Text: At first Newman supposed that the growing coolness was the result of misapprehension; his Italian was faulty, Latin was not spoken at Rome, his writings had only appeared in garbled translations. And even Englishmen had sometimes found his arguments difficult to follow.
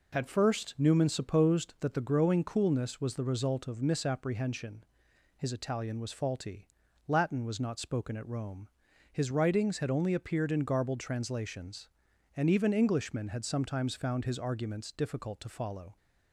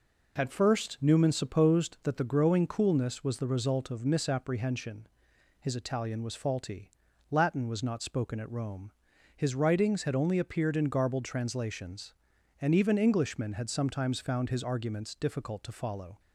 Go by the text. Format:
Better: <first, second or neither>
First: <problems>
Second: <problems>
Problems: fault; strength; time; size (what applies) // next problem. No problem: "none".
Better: neither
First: none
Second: none